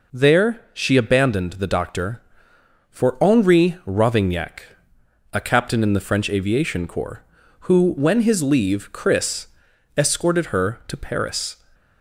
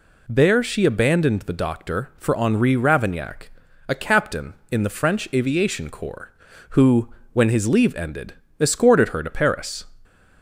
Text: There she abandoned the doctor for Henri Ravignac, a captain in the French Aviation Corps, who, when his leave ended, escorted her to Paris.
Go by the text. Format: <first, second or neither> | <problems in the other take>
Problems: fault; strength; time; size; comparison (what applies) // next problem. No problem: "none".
second | says "chris" for "ended"; at 8.9 s